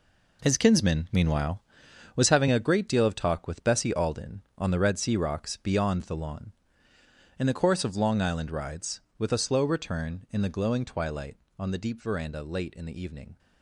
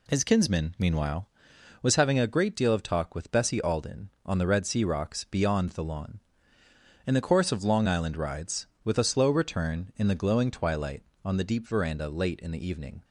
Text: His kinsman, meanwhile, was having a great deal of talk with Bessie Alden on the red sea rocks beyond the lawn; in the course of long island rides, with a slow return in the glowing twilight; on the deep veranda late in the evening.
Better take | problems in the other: second | gets quieter; strong; throughout; 10 dB

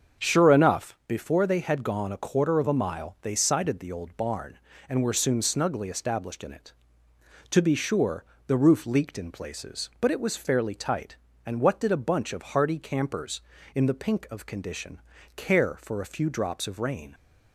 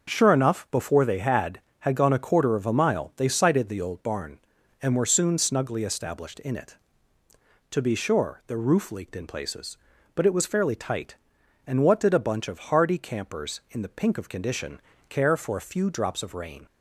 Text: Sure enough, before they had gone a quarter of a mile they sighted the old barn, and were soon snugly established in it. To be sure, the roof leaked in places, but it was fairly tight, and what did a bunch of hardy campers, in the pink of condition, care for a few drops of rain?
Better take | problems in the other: first | starts louder than the rest; until 1.1 s; 6.5 dB; also in the first // says "had" twice; at 1.8 s

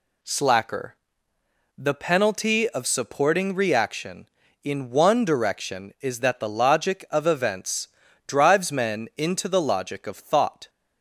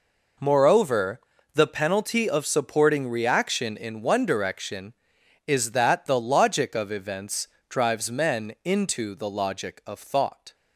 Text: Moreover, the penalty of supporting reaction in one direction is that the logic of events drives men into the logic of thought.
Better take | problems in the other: second | says "Slacker" for "Moreover"; at 0.2 s // pauses between "events" and "drives"; at 7.8 s; 0.40 s long; slight in the second

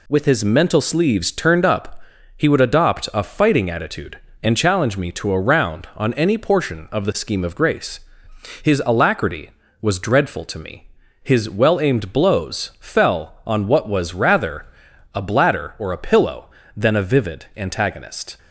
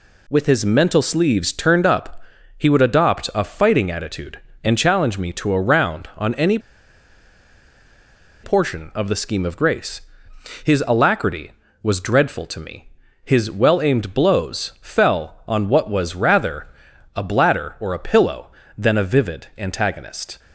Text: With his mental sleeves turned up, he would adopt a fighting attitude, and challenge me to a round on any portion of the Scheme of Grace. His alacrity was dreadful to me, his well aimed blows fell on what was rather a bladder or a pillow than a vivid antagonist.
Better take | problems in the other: first | pauses between "any" and "portion"; strong; at 6.5 s; 1.8 s long // pauses between "rather" and "a"; noticeable; at 16.6 s; 0.48 s long; noticeable in the first

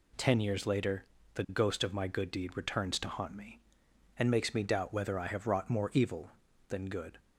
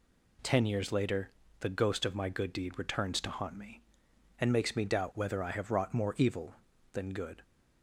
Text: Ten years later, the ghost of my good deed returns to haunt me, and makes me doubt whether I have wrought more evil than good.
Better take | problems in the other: neither | none

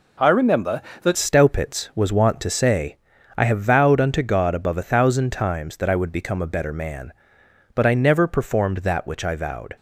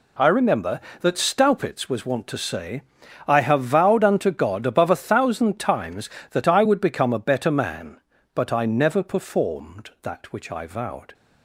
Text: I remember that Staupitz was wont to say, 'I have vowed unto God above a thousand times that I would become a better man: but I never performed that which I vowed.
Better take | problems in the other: second | changes voice at "Staupitz"; from 1.1 s on; 8.6 s long

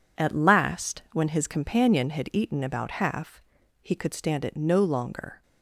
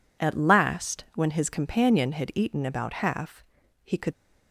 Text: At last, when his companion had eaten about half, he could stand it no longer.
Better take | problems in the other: first | stops before "stand it no longer"; at 4.1 s

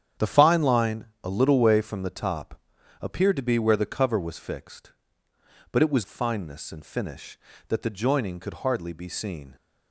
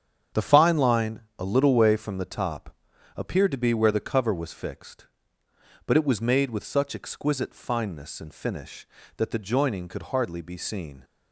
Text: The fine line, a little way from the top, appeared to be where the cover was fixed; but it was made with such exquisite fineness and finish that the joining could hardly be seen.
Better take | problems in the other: second | starts louder than the rest; strong; until 1.3 s; 9 dB; strong in the second // skips "made with such exquisite"; at 6.0 s

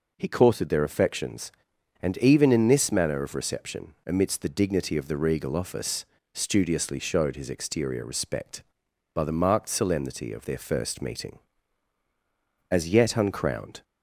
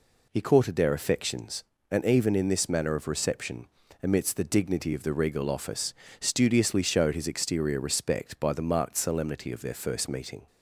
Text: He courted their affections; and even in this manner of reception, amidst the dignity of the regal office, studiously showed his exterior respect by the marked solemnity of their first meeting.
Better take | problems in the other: second | goes on to say "As yet uncrowned"; noticeable; from 12.7 s on; 1.1 s long

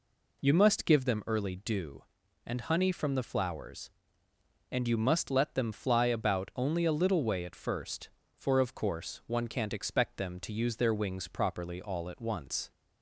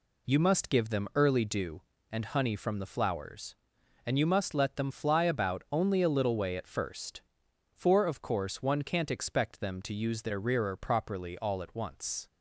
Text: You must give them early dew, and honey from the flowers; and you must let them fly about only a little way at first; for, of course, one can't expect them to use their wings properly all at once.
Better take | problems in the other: first | says "rearer" for "wings"; at 10.4 s

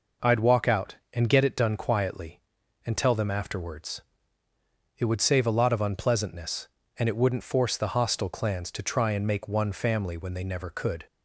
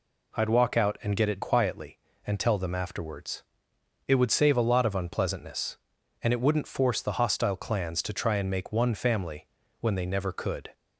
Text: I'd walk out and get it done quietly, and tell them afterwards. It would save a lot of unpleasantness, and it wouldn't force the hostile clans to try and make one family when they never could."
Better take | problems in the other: first | skips "done"; at 1.4 s // pauses between "family" and "when"; slight; at 9.4 s; 0.34 s long

